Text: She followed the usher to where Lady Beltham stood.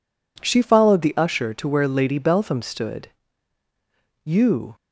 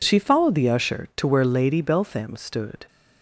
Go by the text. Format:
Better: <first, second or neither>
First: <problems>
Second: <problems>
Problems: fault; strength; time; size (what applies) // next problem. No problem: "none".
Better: second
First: goes on to say "You"; from 4.2 s on; 0.52 s long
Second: none